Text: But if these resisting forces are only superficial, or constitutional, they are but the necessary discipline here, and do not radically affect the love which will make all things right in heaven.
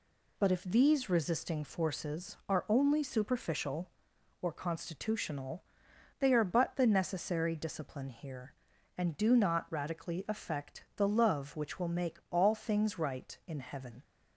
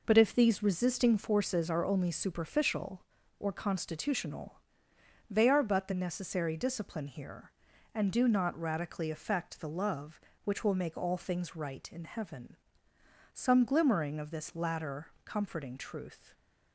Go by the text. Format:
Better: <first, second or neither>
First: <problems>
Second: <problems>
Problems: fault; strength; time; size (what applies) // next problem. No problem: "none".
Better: first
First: none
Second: goes on to say "Some glimmering of this latter comforting truth"; strong; from 13.3 s on; 3.0 s long